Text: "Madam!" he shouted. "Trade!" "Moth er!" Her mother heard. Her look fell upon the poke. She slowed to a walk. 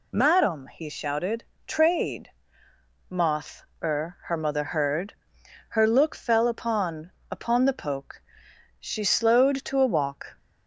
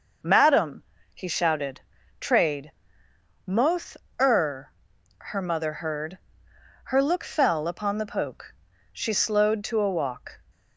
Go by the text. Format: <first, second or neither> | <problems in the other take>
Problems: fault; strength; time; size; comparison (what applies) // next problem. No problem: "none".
second | pauses between "Moth" and "er"; slight; at 3.6 s; 0.22 s long; slight in the second // says "upon" twice; at 7.2 s